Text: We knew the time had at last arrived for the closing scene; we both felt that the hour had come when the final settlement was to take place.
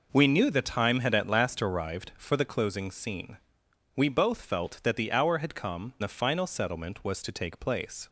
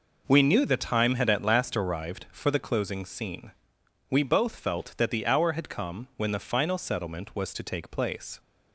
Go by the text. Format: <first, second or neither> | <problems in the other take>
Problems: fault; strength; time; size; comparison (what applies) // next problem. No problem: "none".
second | skips "when"; at 5.9 s